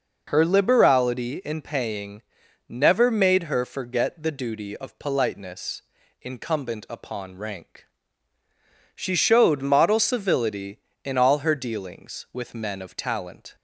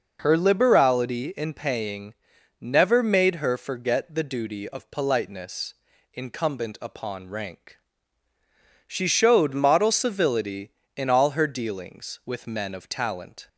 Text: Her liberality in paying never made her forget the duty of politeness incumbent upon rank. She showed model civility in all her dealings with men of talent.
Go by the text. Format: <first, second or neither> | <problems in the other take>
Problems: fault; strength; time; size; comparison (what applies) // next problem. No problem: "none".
neither | pauses between "paying" and "never"; noticeable; the same in both // pauses between "politeness" and "incumbent"; the same in both